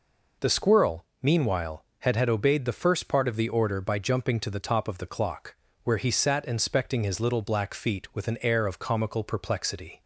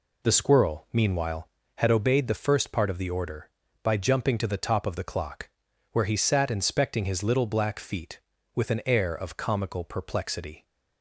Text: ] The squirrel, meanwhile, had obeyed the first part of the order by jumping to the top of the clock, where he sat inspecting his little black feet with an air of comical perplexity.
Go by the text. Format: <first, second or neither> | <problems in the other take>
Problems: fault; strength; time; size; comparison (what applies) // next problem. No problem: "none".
second | says "had" twice; at 2.1 s